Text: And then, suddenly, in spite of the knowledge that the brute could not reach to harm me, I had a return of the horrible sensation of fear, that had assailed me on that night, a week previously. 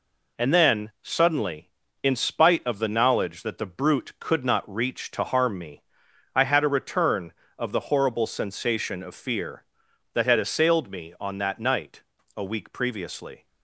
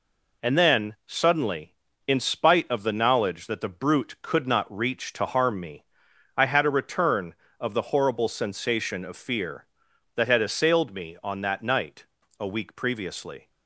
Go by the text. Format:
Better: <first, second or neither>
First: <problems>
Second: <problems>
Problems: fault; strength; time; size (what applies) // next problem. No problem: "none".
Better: neither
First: none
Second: none